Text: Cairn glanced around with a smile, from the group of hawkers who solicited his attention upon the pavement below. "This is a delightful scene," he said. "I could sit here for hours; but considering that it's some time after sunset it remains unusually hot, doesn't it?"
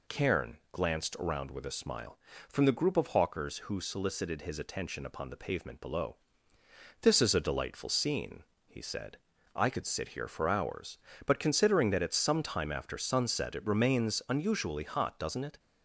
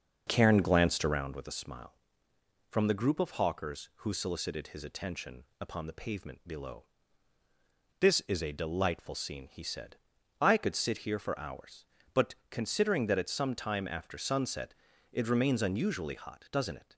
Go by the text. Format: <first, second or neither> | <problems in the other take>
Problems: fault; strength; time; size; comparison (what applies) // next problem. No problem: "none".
first | starts louder than the rest; noticeable; until 1.3 s; 6 dB // pauses between "attention" and "upon"; slight; at 5.4 s; 0.16 s long // pauses between "but" and "considering"; slight; at 12.3 s; 0.16 s long // pauses between "sunset" and "it"; at 14.7 s; 0.38 s long